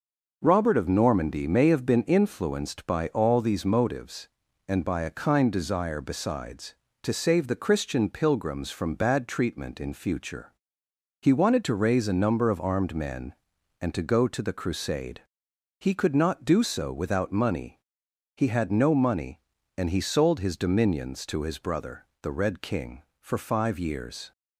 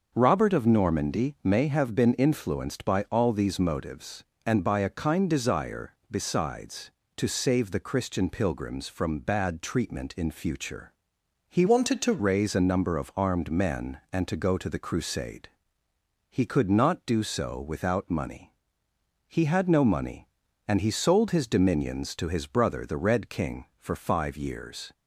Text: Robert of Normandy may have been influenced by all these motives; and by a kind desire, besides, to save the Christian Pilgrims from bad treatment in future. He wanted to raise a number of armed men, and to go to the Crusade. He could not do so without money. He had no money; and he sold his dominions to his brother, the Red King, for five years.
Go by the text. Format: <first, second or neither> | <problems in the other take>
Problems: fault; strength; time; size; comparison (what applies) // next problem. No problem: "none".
first | starts louder than the rest; until 1.1 s; 6 dB // changes voice from "wanted" to "to"; from 11.6 to 12.2 s; 0.6 s long